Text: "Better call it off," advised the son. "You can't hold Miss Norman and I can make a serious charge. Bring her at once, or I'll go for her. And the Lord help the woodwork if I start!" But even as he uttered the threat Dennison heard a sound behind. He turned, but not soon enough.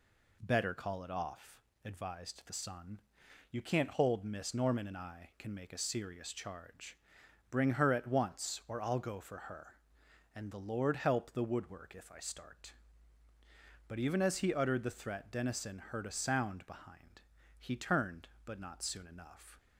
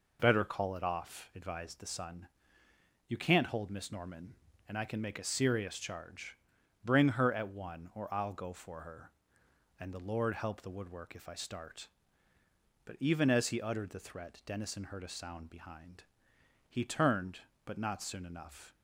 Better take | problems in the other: first | says "one" for "once"; at 7.4 s

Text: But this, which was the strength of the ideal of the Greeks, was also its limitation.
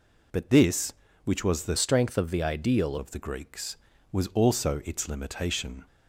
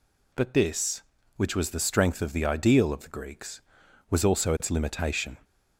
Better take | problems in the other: second | changes voice from "strength" to "ideal"; from 1.7 to 2.9 s; 1.2 s long

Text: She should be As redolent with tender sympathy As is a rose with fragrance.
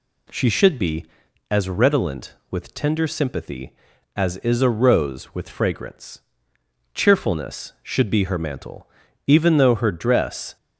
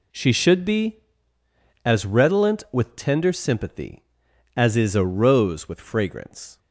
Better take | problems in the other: second | goes on to say "Cheerfulness Should be her mantle even though her dress"; strong; from 6.9 s on; 3.6 s long

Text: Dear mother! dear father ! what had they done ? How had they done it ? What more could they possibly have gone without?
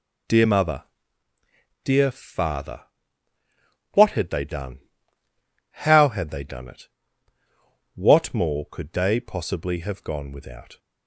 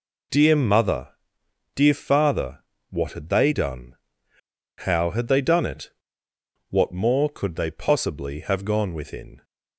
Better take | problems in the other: first | says "within" for "without"; at 8.9 s

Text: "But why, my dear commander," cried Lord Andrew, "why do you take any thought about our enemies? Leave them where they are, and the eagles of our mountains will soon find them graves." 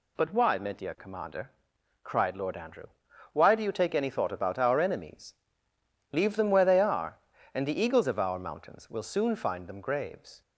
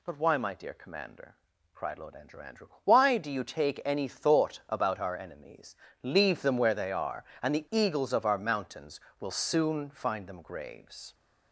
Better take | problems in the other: first | says "Andrew" twice; at 2.4 s

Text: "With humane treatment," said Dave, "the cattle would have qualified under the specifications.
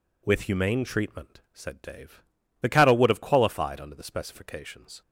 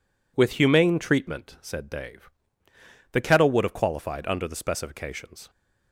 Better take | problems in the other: first | says "kettle" for "cattle"; at 3.1 s

